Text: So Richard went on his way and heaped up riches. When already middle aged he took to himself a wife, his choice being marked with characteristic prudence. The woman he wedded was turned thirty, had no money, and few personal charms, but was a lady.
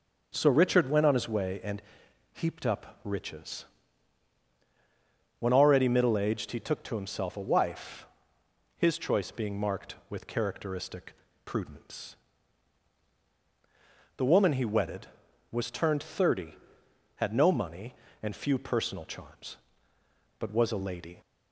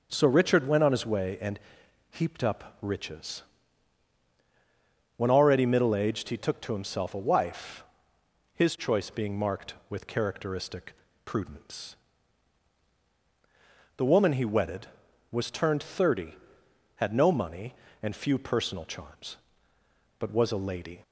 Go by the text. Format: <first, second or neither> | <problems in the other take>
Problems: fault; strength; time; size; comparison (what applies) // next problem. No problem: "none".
neither | pauses between "and" and "heaped"; noticeable; the same in both // pauses between "characteristic" and "prudence"; slight; the same in both